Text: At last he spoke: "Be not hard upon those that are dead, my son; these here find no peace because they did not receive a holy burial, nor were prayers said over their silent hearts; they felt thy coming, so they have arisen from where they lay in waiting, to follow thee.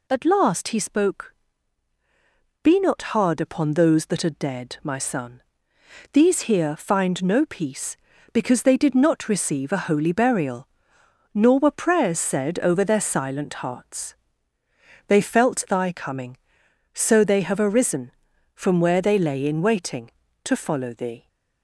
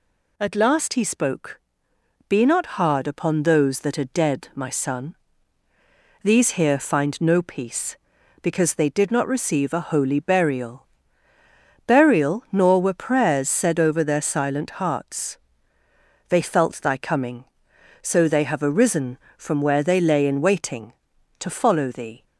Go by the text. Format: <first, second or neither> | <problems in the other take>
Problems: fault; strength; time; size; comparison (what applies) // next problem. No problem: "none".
first | says "burial" twice; at 11.8 s